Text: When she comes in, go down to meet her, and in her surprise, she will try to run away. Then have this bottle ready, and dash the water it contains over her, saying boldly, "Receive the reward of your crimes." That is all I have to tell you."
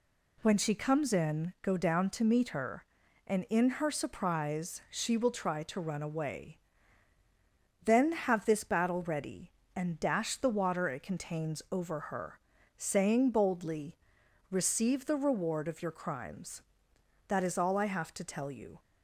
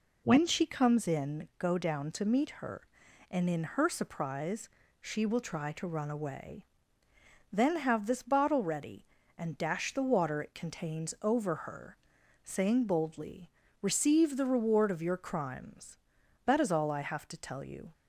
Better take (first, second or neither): second